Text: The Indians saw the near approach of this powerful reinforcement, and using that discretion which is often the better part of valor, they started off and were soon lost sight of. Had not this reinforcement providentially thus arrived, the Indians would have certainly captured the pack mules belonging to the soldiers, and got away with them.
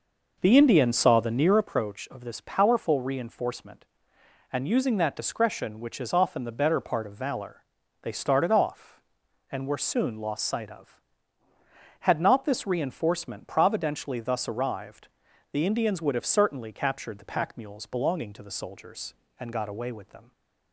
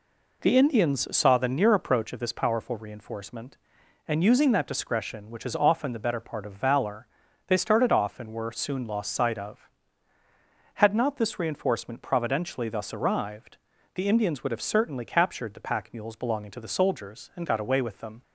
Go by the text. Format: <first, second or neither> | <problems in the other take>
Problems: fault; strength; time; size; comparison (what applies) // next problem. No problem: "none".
second | starts louder than the rest; noticeable; until 1.6 s; 5.5 dB